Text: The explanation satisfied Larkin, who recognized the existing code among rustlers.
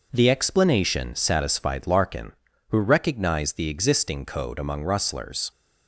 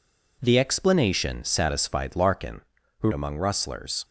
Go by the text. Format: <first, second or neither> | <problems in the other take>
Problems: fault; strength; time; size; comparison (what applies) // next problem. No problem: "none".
first | skips "recognized the existing code"; at 3.1 s